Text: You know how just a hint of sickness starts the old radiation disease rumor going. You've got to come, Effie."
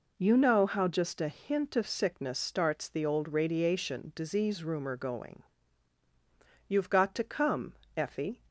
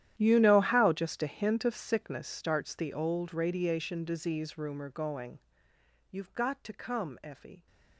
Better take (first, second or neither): first